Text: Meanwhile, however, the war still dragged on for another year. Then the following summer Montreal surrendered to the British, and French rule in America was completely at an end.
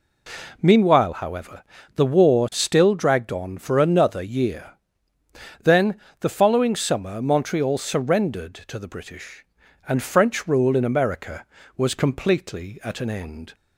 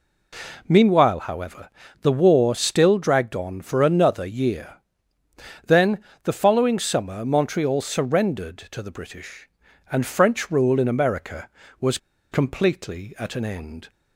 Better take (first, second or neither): first